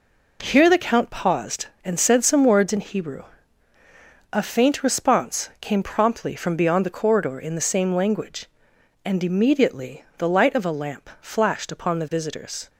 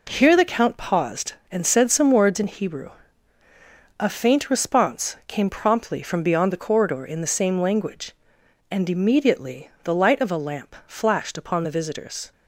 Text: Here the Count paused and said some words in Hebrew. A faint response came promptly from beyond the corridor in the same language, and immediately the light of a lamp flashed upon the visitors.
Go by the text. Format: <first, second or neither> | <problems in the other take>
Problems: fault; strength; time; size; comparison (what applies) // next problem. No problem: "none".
neither | none